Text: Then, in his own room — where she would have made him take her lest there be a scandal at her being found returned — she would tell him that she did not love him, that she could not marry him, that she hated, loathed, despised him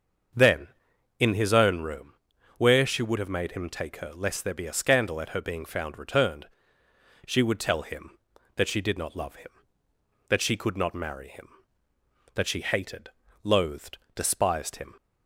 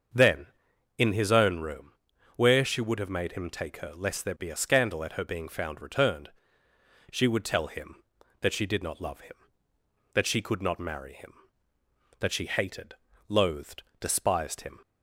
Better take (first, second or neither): neither